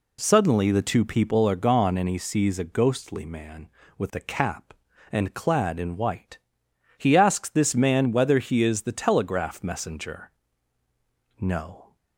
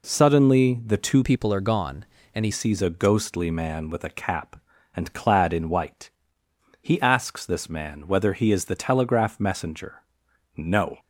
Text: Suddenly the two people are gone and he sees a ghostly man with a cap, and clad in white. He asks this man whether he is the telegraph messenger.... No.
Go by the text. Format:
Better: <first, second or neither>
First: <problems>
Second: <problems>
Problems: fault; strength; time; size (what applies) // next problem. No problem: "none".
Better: first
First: none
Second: changes voice from "people" to "he"; from 1.2 to 2.5 s; 1.3 s long